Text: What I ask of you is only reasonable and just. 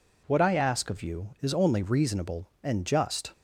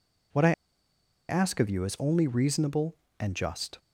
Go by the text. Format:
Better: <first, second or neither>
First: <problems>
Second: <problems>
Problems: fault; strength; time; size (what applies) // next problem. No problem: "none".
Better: first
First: none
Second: pauses between "I" and "ask"; noticeable; at 0.5 s; 0.76 s long